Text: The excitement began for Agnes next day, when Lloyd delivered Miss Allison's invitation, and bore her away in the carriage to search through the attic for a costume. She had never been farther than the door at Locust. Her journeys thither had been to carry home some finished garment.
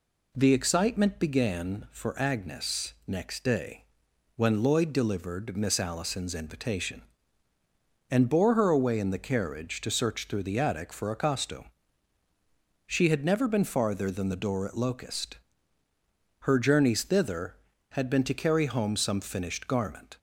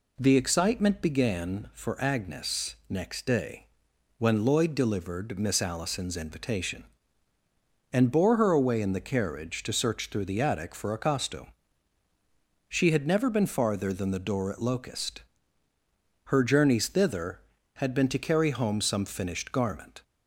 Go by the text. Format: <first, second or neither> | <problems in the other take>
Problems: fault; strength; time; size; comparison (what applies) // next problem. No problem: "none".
neither | none